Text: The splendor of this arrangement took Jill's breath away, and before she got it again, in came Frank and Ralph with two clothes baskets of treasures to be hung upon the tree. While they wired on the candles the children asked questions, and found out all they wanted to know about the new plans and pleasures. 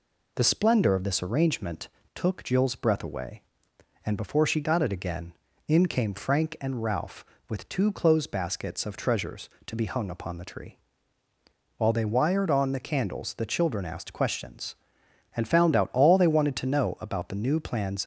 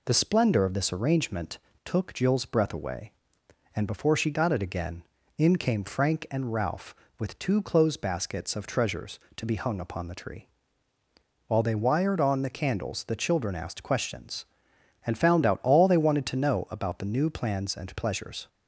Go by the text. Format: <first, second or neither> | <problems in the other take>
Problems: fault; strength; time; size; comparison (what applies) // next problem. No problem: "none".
second | pauses between "arrangement" and "took"; slight; at 1.8 s; 0.28 s long; slight in the second // stops before "and pleasures"; at 18.0 s